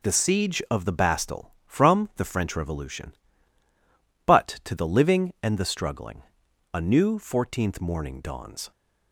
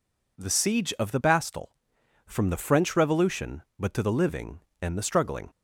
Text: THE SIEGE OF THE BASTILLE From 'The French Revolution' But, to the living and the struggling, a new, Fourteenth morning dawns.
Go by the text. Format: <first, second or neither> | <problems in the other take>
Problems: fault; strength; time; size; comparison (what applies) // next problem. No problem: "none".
first | stops before "a new Fourteenth morning dawns"; at 5.4 s